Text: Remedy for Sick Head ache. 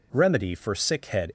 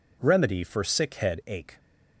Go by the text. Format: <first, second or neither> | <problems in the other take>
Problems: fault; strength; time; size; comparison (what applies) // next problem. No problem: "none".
second | stops before "ache"; at 1.2 s